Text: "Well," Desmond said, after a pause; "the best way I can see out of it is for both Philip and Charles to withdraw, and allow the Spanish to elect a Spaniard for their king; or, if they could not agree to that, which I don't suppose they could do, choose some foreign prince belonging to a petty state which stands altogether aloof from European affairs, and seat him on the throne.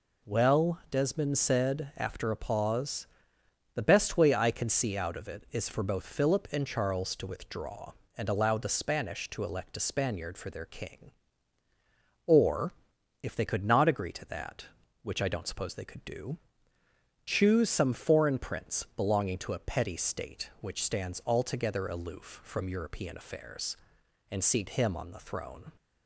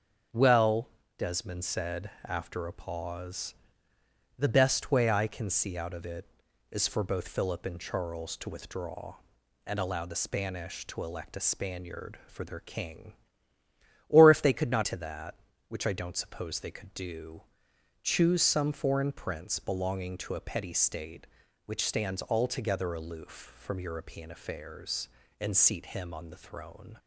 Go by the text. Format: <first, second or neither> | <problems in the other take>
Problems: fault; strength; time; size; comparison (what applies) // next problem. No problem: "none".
first | skips "agree"; at 14.8 s